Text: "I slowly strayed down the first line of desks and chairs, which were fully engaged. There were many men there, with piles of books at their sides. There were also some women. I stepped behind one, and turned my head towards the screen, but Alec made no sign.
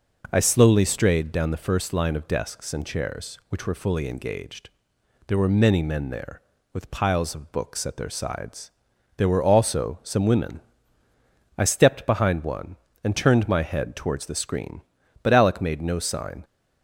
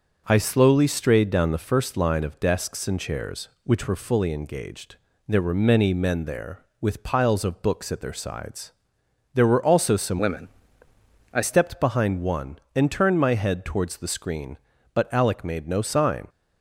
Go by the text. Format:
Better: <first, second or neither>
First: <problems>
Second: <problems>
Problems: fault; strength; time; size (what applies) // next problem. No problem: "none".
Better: first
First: none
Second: changes voice from "women" to "I"; from 10.1 to 11.4 s; 1.3 s long